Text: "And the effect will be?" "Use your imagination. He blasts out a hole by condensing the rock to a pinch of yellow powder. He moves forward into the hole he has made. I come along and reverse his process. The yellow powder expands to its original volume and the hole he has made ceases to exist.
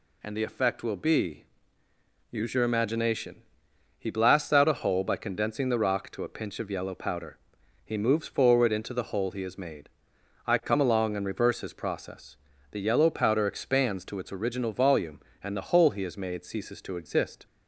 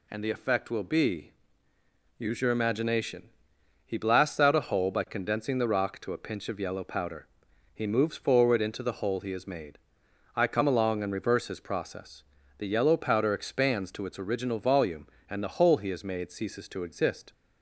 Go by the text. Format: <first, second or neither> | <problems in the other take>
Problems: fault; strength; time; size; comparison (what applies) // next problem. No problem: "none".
neither | none